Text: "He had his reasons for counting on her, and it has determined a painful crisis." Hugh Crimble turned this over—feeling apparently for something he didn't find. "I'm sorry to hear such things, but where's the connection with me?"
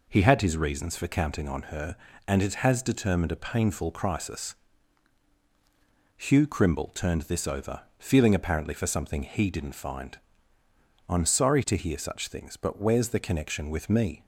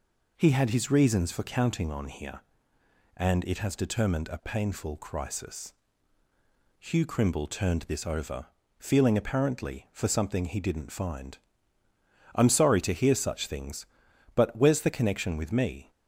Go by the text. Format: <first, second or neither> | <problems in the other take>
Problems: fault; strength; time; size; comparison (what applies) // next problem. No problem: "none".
first | says "here" for "her"; at 2.0 s